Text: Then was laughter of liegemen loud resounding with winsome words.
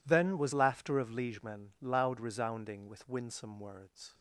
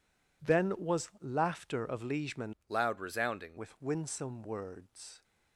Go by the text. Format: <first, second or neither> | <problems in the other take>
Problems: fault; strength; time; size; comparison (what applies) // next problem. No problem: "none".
first | changes voice from "loud" to "resounding"; from 2.6 to 3.5 s; 0.9 s long